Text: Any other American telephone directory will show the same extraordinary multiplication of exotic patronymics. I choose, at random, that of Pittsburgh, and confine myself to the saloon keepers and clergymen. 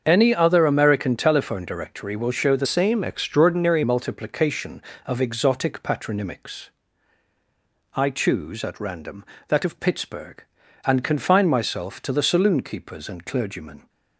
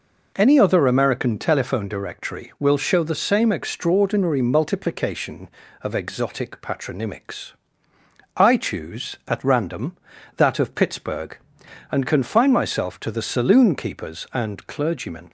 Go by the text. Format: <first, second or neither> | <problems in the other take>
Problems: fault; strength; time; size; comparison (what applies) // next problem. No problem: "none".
second | starts louder than the rest; until 1.0 s; 7 dB // changes voice from "same" to "extraordinary"; from 2.6 to 3.8 s; 1.2 s long